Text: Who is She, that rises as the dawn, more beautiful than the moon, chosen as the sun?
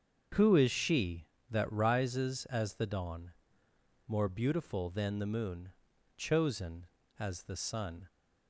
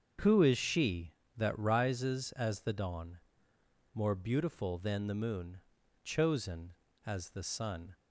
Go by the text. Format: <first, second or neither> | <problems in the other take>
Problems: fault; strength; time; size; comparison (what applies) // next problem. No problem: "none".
neither | starts louder than the rest; strong; the same in both